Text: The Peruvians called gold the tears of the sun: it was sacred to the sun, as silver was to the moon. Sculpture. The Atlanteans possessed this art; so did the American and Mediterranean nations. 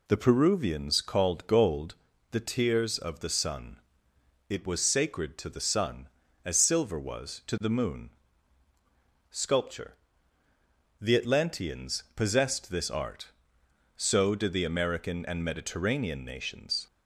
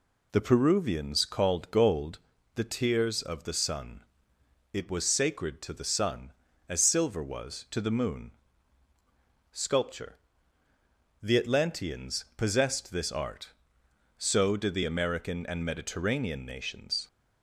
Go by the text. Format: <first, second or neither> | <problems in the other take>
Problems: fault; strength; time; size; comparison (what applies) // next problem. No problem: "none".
neither | pauses between "gold" and "the"; slight; the same in both